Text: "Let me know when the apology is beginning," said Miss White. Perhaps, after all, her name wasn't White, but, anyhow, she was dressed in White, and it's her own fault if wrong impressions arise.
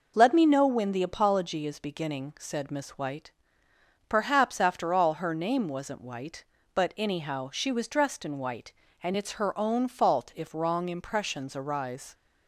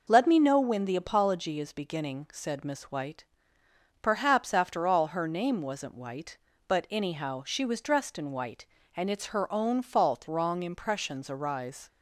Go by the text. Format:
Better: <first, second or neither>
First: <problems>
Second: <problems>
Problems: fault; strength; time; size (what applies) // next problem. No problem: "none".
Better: first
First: none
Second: skips "if"; at 10.2 s